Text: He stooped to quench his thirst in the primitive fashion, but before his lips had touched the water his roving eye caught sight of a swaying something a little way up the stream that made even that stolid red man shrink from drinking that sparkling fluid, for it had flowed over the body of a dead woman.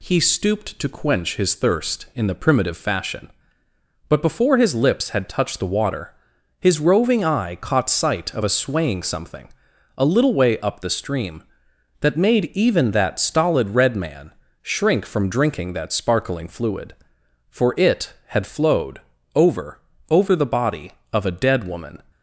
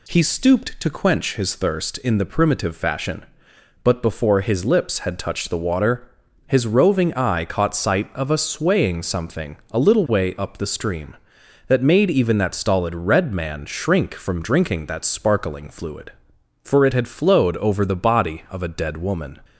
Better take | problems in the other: second | pauses between "water" and "his"; noticeable; at 6.1 s; 0.48 s long; also in the second // pauses between "something" and "a"; noticeable; at 9.5 s; 0.46 s long // pauses between "man" and "shrink"; slight; at 14.3 s; 0.30 s long // pauses between "flowed" and "over"; slight; at 19.0 s; 0.32 s long // says "over" twice; at 20.0 s

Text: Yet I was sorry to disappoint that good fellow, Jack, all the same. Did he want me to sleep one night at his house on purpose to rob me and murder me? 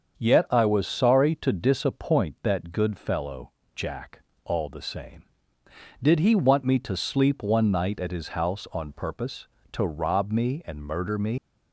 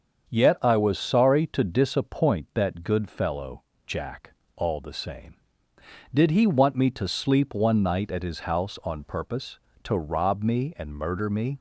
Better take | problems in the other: second | starts louder than the rest; until 1.1 s; 7 dB; also in the second // leaves "me" unfinished; at 11.3 s; 85 ms

